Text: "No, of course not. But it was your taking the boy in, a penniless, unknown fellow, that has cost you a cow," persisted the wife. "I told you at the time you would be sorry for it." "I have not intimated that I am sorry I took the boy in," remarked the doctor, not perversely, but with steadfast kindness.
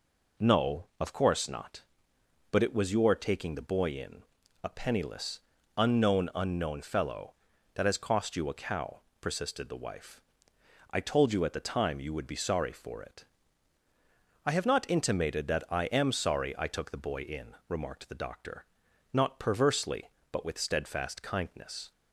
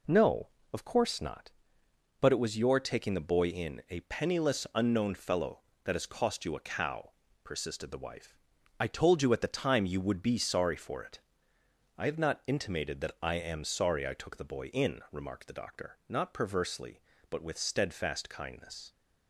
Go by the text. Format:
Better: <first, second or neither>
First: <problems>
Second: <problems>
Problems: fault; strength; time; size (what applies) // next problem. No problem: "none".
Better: second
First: says "unknown" twice; at 6.3 s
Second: none